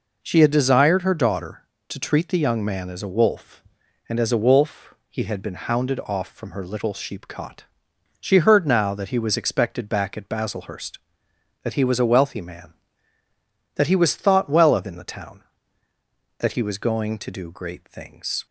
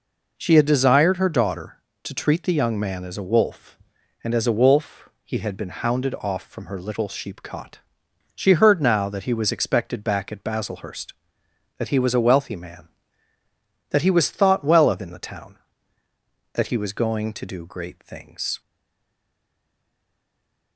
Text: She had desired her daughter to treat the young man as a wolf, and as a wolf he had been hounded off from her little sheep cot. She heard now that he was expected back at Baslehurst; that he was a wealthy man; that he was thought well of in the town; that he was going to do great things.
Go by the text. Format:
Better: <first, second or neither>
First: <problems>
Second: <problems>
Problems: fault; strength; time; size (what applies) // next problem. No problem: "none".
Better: first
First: pauses between "wolf" and "he"; slight; at 4.9 s; 0.16 s long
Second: pauses between "wolf" and "he"; slight; at 5.0 s; 0.16 s long // stays silent after the last word; from 18.6 s on; 2.1 s long